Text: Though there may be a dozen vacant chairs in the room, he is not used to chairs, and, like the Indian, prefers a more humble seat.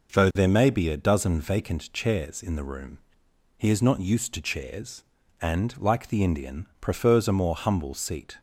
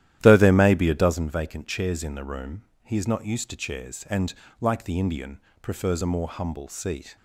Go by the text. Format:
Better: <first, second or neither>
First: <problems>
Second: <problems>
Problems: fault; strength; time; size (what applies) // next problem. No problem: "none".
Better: first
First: none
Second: starts louder than the rest; strong; until 1.2 s; 12.5 dB